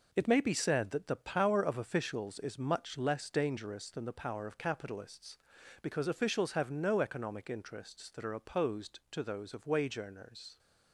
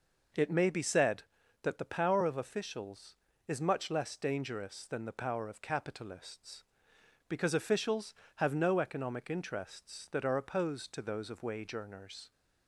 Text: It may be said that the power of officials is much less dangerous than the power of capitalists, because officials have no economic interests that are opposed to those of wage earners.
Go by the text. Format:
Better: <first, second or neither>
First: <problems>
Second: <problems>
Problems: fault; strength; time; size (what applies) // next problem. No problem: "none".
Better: second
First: gets quieter; strong; throughout; 7 dB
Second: none